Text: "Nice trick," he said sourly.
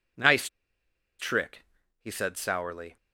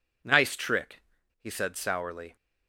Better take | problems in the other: second | pauses between "Nice" and "trick"; noticeable; at 0.4 s; 0.72 s long

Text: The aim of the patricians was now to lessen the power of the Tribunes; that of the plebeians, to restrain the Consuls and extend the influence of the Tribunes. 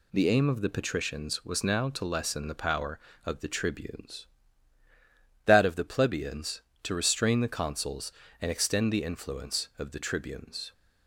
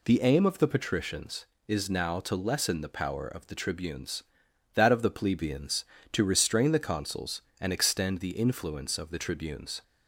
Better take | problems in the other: first | says "is" for "was"; at 1.6 s

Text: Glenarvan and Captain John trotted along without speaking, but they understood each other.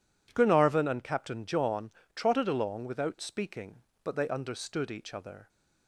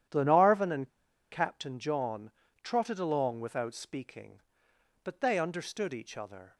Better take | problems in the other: first | starts louder than the rest; strong; until 1.5 s; 10.5 dB // pauses between "and" and "Captain"; at 0.8 s; 0.44 s long // pauses between "John" and "trotted"; slight; at 2.3 s; 0.32 s long; slight in the first

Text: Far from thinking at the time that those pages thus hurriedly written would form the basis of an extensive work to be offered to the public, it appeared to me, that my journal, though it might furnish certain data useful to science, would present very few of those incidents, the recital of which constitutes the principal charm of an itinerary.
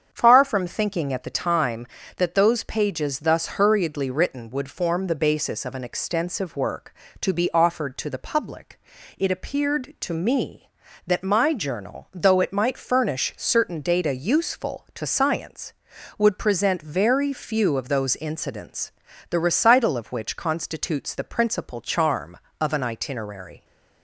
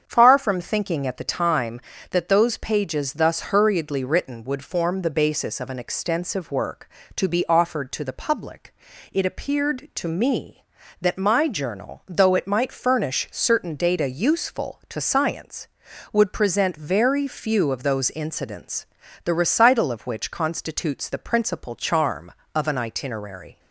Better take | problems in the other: neither | starts louder than the rest; strong; the same in both

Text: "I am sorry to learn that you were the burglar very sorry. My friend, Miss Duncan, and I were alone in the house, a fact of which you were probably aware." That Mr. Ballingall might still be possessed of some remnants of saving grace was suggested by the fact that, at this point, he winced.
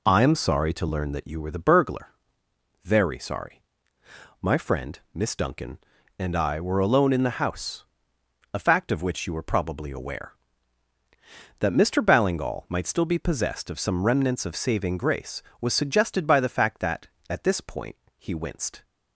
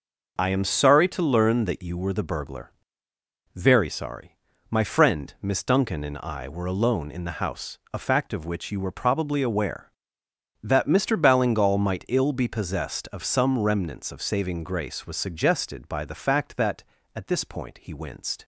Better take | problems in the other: first | pauses between "burglar" and "very"; noticeable; at 2.7 s; 0.84 s long; noticeable in the first // says "ill" for "still"; at 12.0 s

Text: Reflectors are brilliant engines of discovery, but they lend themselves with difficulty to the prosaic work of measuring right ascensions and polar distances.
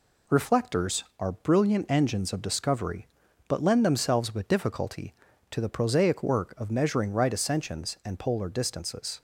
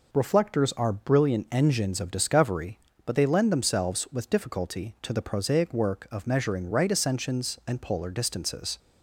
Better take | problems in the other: second | skips "they"; at 3.6 s

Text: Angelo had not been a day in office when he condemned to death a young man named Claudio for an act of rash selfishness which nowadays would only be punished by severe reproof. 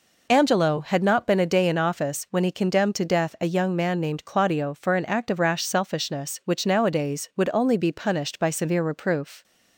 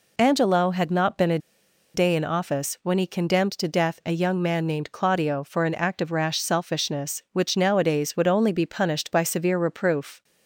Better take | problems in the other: first | pauses between "a" and "day"; noticeable; at 1.3 s; 0.56 s long

